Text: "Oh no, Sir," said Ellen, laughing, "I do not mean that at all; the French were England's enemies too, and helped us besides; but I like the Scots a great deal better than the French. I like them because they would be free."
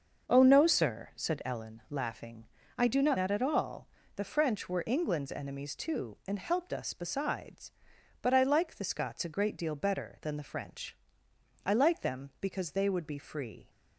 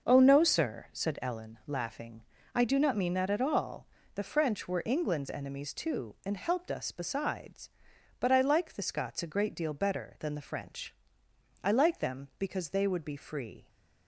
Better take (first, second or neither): second